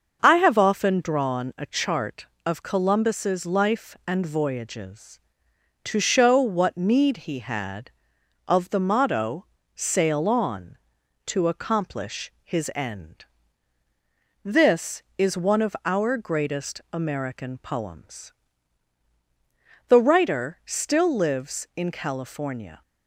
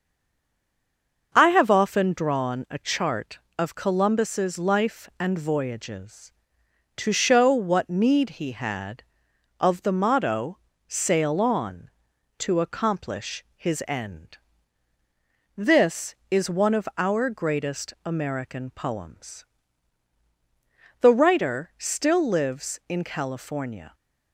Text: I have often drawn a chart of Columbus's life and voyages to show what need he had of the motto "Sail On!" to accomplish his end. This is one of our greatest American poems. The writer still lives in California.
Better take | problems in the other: first | stays silent before the first word; noticeable; until 1.3 s; 1.3 s long // starts louder than the rest; until 2.3 s; 6.5 dB; also in the first // pauses between "motto" and "Sail"; slight; at 10.5 s; 0.30 s long; slight in the first

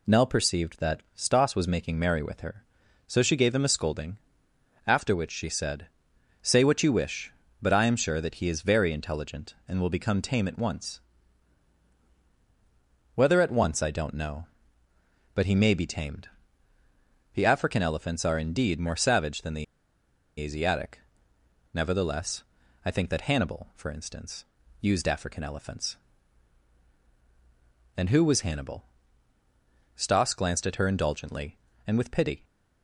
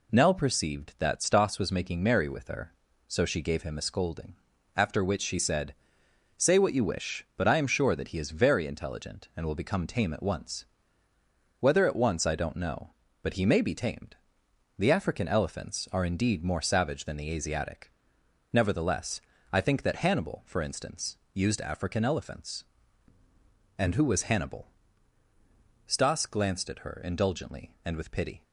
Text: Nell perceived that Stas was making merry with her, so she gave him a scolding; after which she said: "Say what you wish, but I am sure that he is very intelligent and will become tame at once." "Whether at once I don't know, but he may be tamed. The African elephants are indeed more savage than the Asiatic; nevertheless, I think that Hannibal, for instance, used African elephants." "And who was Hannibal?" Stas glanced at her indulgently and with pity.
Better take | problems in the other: second | pauses between "the" and "Asiatic"; noticeable; at 19.6 s; 0.76 s long

